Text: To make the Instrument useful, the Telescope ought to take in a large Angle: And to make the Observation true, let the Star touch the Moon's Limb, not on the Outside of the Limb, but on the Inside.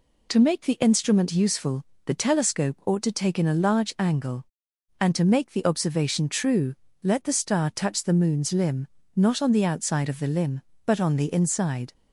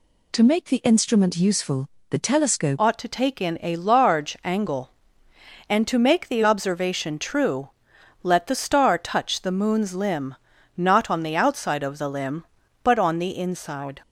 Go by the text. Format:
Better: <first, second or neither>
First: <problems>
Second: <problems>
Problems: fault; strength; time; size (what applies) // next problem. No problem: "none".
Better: first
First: none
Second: changes voice at "ought"; from 2.7 s on; 11.3 s long